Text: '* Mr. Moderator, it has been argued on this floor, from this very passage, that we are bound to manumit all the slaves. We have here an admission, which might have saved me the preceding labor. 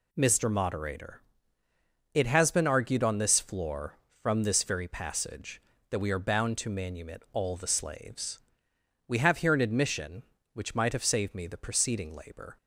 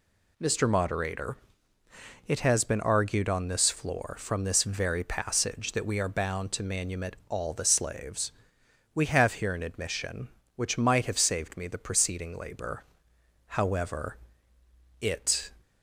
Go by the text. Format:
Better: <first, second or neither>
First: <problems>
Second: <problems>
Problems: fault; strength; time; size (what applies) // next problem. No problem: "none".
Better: first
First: none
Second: pauses between "manumit" and "all"; slight; at 7.1 s; 0.16 s long // goes on to say "However it"; strong; from 13.4 s on; 2.0 s long